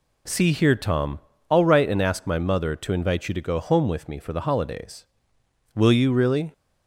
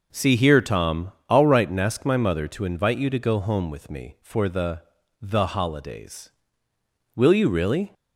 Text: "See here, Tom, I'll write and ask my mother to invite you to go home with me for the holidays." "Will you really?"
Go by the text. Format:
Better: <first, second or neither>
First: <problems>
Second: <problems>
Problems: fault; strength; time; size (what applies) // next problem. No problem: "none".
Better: first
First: none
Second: says "the" twice; at 5.2 s